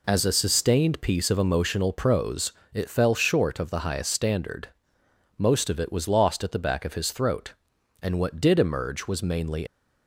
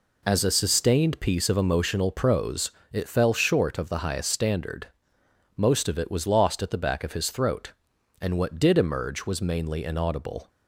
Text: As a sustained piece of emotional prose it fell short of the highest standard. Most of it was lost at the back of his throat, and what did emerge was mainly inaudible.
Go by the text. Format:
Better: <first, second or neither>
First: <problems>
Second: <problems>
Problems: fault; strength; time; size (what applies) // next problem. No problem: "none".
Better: second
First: pauses between "prose" and "it"; slight; at 2.5 s; 0.24 s long // stops before "inaudible"; at 9.6 s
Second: pauses between "prose" and "it"; slight; at 2.6 s; 0.24 s long